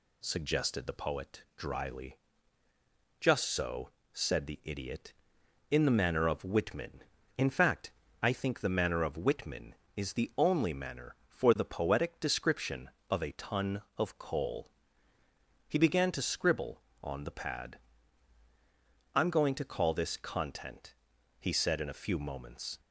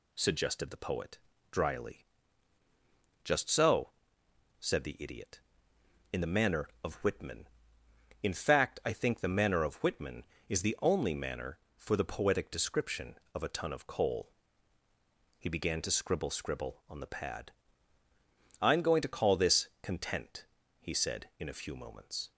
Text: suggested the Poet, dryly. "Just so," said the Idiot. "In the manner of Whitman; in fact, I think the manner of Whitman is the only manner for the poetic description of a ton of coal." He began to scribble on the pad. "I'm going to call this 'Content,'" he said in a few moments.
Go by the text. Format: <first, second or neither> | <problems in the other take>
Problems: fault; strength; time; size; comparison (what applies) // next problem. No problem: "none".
first | says "scribble" twice; at 16.2 s